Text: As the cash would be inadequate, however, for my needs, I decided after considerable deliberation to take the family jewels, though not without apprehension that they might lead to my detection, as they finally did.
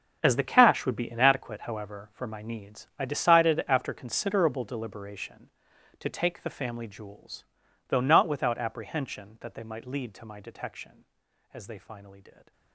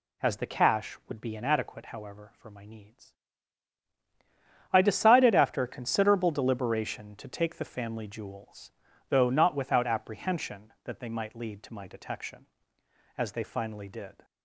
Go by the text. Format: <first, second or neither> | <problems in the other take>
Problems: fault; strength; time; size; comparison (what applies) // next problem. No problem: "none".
second | gets quieter; strong; throughout; 15 dB